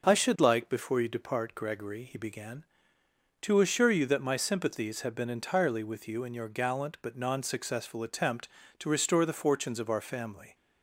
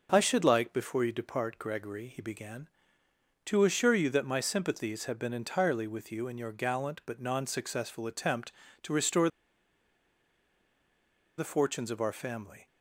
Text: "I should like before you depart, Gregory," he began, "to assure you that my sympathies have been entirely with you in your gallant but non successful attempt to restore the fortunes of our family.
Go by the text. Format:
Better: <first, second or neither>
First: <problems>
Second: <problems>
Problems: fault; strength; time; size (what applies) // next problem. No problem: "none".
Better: first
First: none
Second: pauses between "restore" and "the"; strong; at 9.2 s; 2.0 s long